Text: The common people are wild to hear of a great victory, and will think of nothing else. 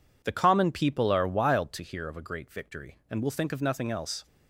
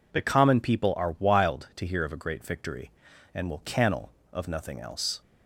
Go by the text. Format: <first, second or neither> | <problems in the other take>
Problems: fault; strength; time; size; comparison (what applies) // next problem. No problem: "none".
first | says "cannel" for "think"; at 3.6 s